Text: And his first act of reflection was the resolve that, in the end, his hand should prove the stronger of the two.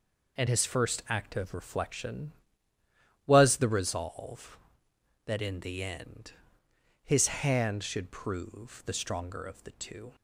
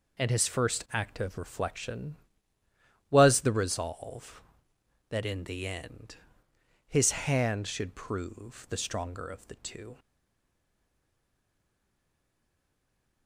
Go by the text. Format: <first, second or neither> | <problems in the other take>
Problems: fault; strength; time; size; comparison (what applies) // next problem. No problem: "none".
first | stays silent after the last word; strong; from 9.9 s on; 3.3 s long